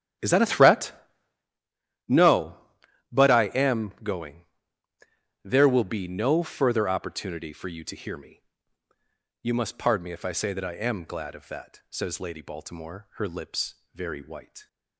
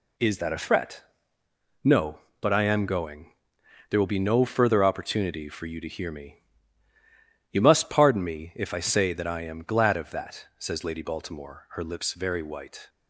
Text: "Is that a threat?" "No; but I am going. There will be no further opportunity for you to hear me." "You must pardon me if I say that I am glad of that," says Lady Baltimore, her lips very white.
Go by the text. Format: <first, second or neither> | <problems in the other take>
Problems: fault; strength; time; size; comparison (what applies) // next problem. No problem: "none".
second | starts louder than the rest; strong; until 1.6 s; 11 dB // pauses between "lips" and "very"; slight; at 13.7 s; 0.18 s long